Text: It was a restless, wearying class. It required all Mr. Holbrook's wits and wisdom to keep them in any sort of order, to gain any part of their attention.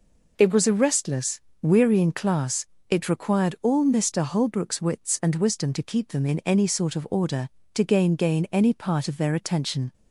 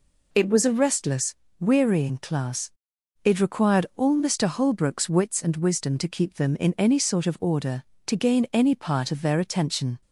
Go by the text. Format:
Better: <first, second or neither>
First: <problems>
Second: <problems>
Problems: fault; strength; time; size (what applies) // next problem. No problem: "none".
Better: second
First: says "gain" twice; at 8.1 s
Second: none